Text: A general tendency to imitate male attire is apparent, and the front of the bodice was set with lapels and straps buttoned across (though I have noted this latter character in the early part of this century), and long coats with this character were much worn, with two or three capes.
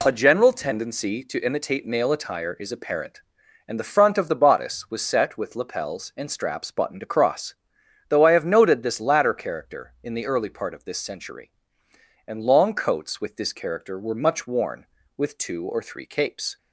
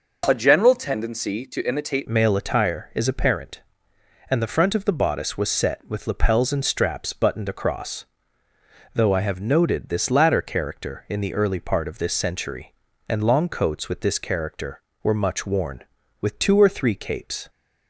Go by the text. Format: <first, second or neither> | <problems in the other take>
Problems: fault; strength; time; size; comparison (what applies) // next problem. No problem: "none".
first | changes voice at "male"; from 2.0 s on; 15.4 s long